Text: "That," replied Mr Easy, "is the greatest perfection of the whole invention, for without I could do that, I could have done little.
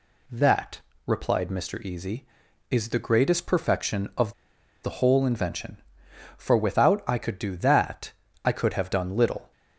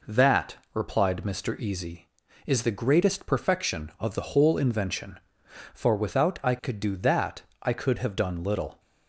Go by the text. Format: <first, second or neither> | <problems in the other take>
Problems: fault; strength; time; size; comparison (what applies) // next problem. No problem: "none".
second | pauses between "of" and "the"; noticeable; at 4.3 s; 0.50 s long